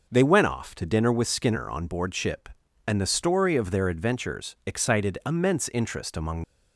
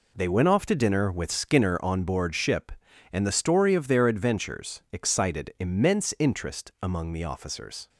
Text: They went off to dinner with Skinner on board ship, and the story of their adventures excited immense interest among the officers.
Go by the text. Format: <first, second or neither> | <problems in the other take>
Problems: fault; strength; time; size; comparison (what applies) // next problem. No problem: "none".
second | stops before "the officers"; at 6.4 s